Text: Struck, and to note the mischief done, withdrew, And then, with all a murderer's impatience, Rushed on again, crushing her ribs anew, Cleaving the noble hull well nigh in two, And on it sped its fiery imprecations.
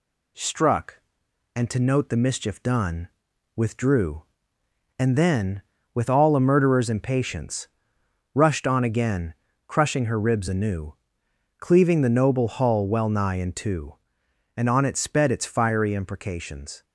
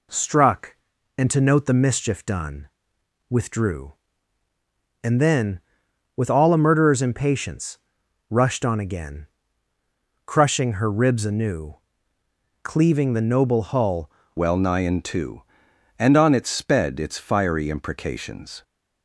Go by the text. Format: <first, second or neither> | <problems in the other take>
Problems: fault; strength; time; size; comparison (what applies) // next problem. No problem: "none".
first | changes voice at "well"; from 14.3 s on; 4.3 s long